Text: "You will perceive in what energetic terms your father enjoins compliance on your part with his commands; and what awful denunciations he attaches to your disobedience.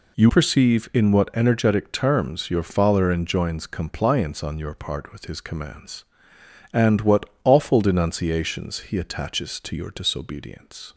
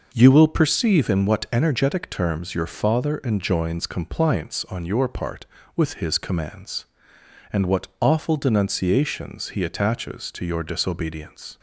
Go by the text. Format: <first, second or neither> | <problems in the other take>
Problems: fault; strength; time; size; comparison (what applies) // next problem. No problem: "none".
second | skips "will"; at 0.2 s // pauses between "what" and "awful"; slight; at 7.2 s; 0.18 s long